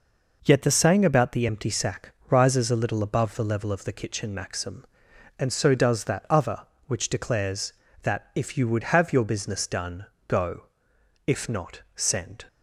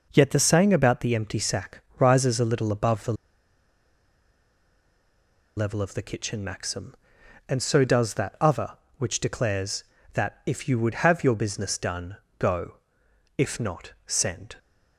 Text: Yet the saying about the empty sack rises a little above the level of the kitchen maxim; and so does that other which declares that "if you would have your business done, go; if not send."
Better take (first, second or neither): first